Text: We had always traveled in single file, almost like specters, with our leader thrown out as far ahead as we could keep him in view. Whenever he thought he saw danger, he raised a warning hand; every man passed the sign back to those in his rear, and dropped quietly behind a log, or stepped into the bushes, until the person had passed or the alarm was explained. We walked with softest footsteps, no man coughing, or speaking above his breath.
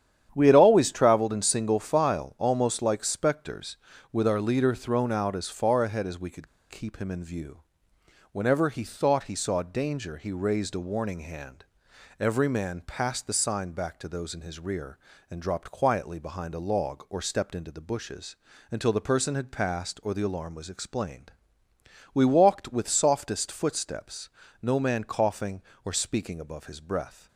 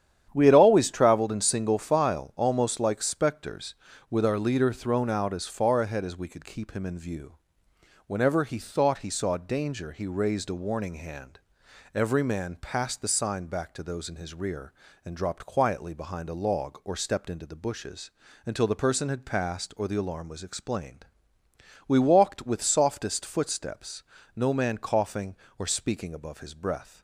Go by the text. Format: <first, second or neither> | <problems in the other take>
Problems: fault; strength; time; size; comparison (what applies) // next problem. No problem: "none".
second | starts louder than the rest; strong; until 1.3 s; 9.5 dB; strong in the second // pauses between "could" and "keep"; slight; at 6.4 s; 0.24 s long